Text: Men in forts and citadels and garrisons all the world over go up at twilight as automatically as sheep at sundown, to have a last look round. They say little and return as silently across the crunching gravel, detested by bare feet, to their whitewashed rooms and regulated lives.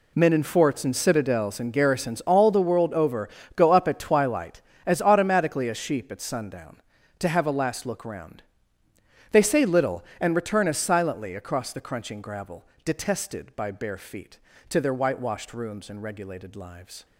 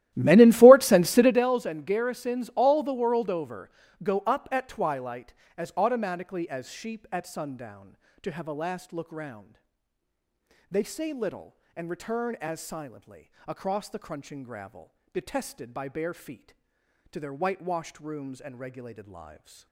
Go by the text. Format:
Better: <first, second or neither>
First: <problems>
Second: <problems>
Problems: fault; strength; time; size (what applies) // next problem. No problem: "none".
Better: first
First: pauses between "over" and "go"; slight; at 3.2 s; 0.26 s long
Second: starts louder than the rest; strong; until 1.5 s; 14.5 dB // pauses between "over" and "go"; slight; at 3.7 s; 0.32 s long // pauses between "silently" and "across"; slight; at 13.3 s; 0.18 s long